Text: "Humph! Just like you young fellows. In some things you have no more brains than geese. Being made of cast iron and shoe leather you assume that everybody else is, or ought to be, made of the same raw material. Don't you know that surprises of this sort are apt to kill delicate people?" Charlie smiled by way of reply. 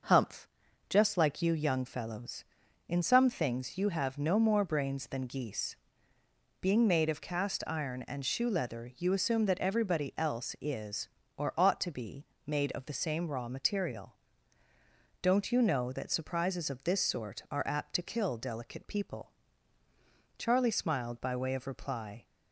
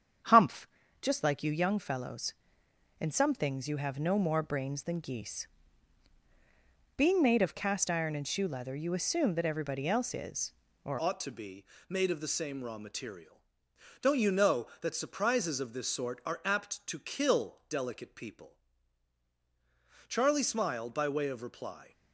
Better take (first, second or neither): first